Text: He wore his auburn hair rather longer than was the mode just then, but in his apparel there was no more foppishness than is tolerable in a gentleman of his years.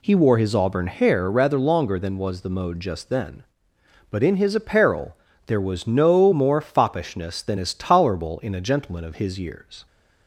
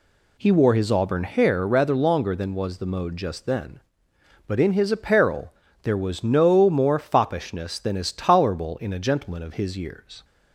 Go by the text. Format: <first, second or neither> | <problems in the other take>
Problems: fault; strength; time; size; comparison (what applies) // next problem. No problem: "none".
neither | pauses between "apparel" and "there"; slight; the same in both